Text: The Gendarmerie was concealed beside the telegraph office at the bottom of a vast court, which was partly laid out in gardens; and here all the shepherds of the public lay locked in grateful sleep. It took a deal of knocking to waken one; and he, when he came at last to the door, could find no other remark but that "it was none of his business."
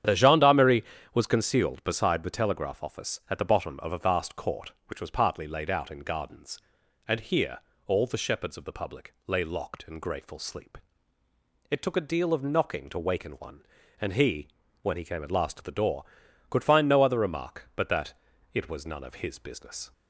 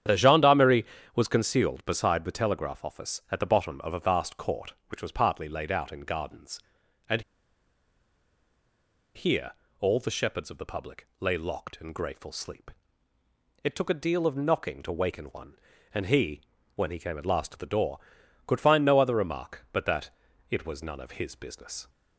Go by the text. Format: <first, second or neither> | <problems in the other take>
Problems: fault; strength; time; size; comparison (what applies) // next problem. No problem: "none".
first | starts louder than the rest; strong; until 1.3 s; 9.5 dB; strong in the first // pauses between "and" and "here"; strong; at 7.2 s; 1.9 s long // pauses between "here" and "all"; slight; at 9.5 s; 0.30 s long; slight in the first // pauses between "that" and "it"; at 20.0 s; 0.40 s long; also in the first